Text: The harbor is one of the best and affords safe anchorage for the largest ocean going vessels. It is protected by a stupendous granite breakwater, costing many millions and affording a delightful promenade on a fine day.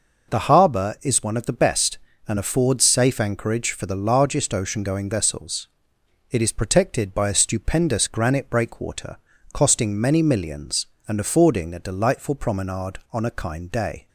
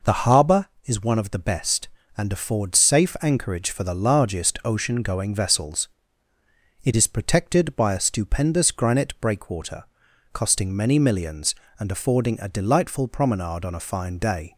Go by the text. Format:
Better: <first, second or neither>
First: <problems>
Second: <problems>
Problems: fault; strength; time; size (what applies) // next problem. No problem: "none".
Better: second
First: says "kind" for "fine"; at 13.2 s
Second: none